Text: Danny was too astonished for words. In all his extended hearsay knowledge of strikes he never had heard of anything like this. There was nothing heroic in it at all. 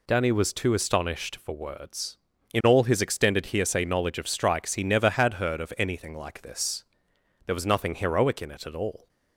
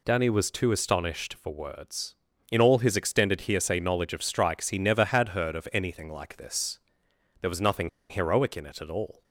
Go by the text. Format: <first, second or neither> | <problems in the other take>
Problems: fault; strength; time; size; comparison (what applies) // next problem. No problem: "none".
first | pauses between "nothing" and "heroic"; slight; at 7.8 s; 0.21 s long